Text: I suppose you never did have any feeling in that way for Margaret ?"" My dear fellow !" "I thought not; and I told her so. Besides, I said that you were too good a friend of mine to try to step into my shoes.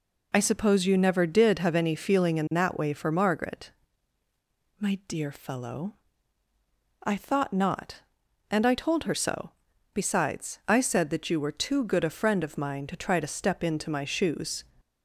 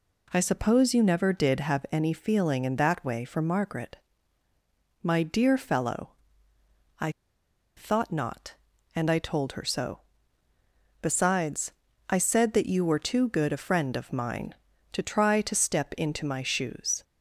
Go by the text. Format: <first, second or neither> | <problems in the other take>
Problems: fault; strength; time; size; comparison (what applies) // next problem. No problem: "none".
first | pauses between "I" and "thought"; noticeable; at 7.1 s; 0.65 s long